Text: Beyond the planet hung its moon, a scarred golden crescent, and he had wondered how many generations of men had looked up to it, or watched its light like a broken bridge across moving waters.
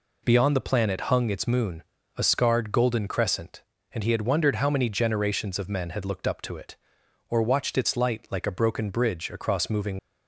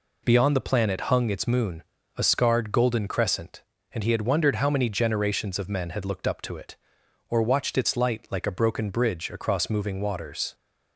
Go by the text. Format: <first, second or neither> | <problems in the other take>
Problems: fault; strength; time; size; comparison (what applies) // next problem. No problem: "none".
second | stops before "waters"; at 9.9 s